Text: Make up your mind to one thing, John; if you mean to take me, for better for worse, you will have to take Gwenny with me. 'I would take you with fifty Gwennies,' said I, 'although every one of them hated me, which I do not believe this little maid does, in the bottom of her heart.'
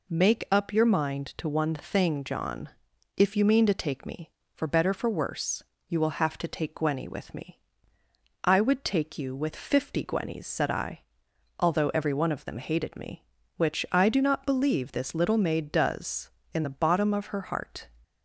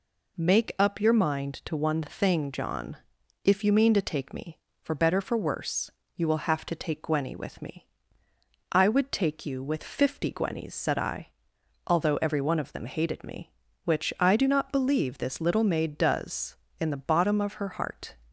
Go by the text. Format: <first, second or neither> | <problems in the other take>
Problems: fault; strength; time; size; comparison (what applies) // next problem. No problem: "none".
neither | none